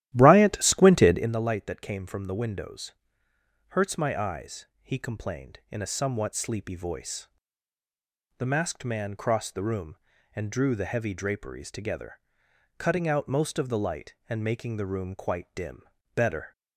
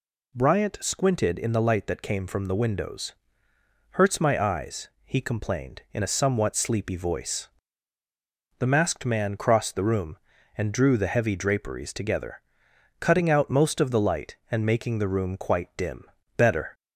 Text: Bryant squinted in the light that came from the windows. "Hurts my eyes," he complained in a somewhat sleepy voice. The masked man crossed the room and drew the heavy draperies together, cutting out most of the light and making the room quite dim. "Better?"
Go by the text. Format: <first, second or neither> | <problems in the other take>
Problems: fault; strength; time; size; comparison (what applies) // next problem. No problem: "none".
second | starts louder than the rest; strong; until 1.3 s; 13.5 dB